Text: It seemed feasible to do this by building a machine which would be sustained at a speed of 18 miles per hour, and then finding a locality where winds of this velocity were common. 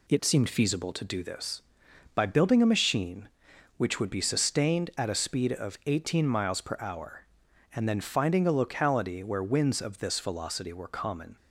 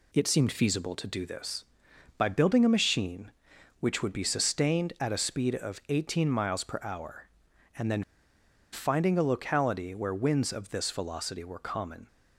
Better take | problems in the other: first | pauses between "then" and "finding"; noticeable; at 8.0 s; 0.69 s long

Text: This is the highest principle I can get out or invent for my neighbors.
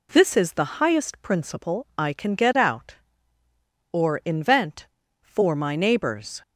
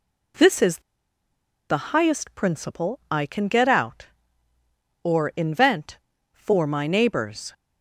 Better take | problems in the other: first | pauses between "is" and "the"; noticeable; at 0.7 s; 0.90 s long

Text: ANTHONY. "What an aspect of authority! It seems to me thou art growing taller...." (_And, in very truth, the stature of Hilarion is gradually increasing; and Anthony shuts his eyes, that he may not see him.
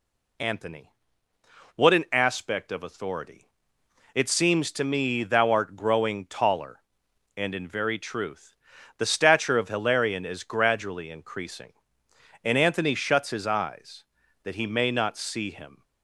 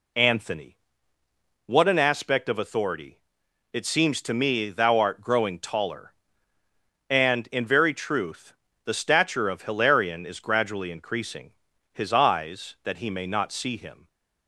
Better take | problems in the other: first | skips "and Anthony shuts"; at 11.7 s

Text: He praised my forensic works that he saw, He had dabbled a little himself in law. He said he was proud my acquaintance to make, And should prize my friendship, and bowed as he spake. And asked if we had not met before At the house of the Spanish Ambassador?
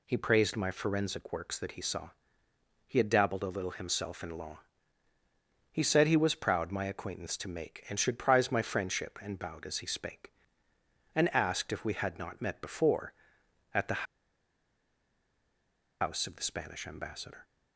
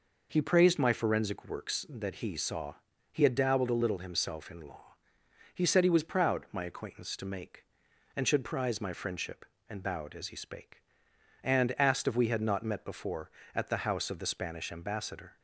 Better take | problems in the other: second | pauses between "the" and "house"; strong; at 14.0 s; 1.9 s long

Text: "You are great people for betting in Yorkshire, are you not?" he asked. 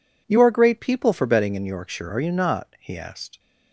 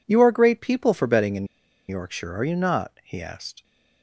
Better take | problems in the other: first | pauses between "in" and "Yorkshire"; at 1.4 s; 0.43 s long

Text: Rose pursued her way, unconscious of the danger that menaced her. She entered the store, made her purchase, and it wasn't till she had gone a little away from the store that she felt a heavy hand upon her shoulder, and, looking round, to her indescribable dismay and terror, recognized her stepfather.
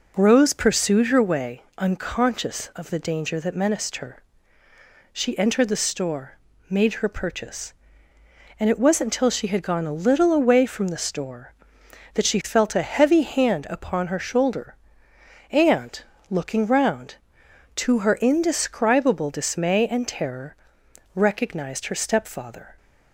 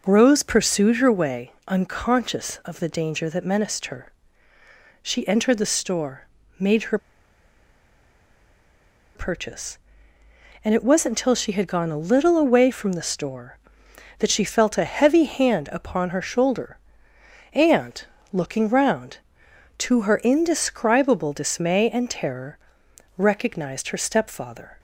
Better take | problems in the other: first | pauses between "her" and "purchase"; strong; at 6.9 s; 2.1 s long

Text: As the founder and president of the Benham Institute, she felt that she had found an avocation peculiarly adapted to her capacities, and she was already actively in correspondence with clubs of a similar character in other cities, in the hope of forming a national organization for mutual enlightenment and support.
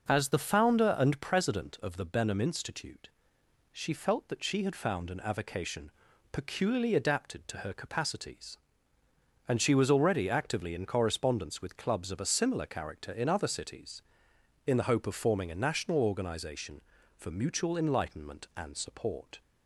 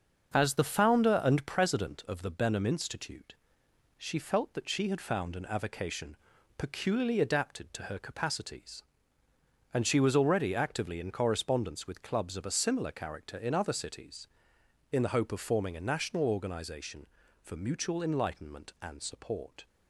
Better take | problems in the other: first | gets quieter; noticeable; throughout; 5.5 dB // pauses between "avocation" and "peculiarly"; at 6.1 s; 0.40 s long; also in the first

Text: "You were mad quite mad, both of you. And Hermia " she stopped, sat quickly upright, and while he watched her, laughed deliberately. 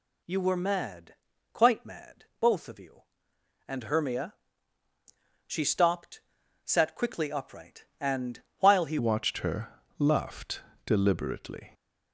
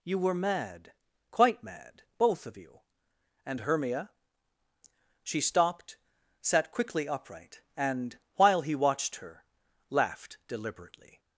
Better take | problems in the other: second | pauses between "mad" and "quite"; at 1.1 s; 0.38 s long; also in the second // pauses between "and" and "while"; slight; at 8.4 s; 0.18 s long; slight in the second // changes voice at "watched"; from 8.9 s on; 2.8 s long // pauses between "laughed" and "deliberately"; slight; at 10.6 s; 0.22 s long

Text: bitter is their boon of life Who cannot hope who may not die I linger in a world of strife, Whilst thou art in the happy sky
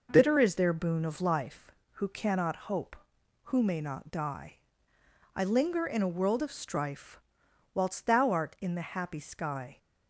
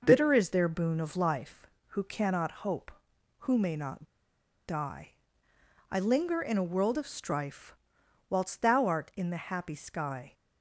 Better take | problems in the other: first | pauses between "not" and "die"; noticeable; at 4.0 s; 0.61 s long // pauses between "die" and "I"; noticeable; at 5.0 s; 0.82 s long; noticeable in the first

